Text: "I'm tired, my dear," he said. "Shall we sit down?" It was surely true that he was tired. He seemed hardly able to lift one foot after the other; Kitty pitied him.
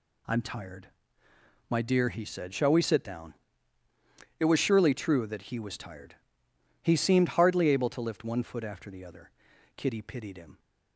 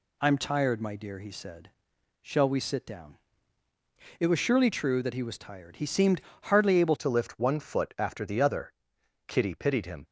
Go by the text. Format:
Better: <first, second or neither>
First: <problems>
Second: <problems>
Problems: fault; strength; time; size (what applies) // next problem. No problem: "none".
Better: first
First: none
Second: pauses between "seemed" and "hardly"; slight; at 6.2 s; 0.22 s long // changes voice at "to"; from 6.9 s on; 3.1 s long